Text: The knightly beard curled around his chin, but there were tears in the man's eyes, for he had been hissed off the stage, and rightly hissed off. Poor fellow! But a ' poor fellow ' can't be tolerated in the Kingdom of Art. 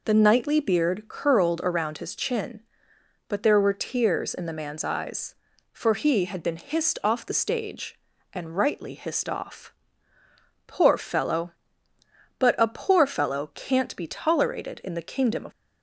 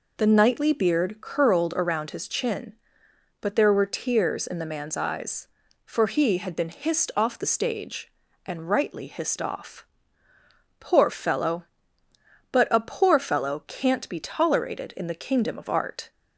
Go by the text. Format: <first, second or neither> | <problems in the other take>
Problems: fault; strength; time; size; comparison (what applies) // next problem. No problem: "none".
second | stops before "Art"; at 15.5 s